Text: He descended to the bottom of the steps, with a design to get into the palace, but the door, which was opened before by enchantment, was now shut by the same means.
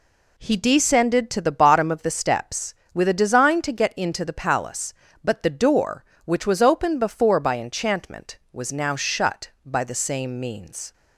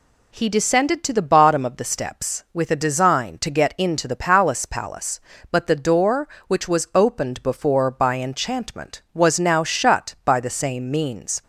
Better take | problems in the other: first | says "palace" twice; at 4.6 s

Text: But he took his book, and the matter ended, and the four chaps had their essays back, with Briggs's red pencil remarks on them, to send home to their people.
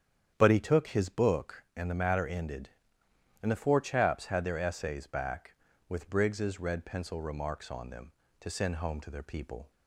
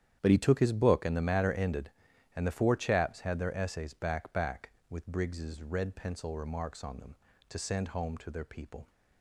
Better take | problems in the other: first | starts louder than the rest; strong; until 1.2 s; 10 dB; strong in the first // says "back" twice; at 4.3 s

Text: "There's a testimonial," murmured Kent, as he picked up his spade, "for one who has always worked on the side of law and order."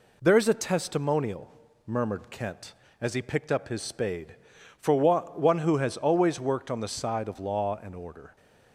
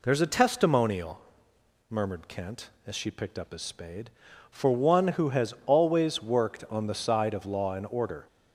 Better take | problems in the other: first | says "she" for "he"; at 2.9 s

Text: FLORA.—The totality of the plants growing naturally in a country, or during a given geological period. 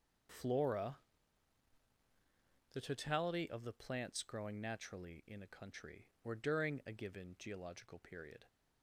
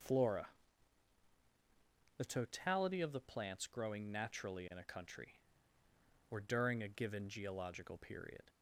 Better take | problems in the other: neither | none

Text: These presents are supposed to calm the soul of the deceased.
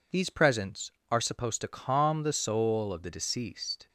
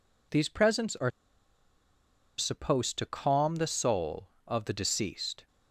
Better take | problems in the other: first | pauses between "are" and "supposed"; strong; at 1.0 s; 1.2 s long

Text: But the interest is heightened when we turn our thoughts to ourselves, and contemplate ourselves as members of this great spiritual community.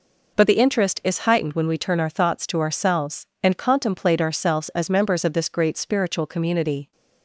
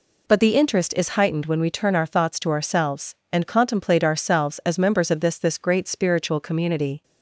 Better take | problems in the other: first | says "this" twice; at 5.3 s

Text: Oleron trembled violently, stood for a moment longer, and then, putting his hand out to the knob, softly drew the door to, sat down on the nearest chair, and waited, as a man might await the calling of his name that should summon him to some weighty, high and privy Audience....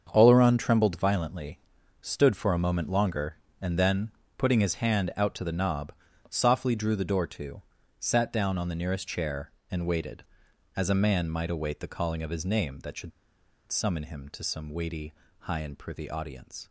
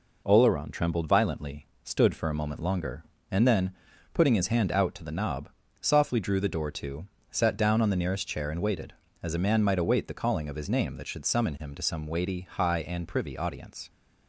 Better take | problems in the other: second | starts louder than the rest; until 1.1 s; 7 dB // pauses between "should" and "summon"; noticeable; at 13.1 s; 0.59 s long

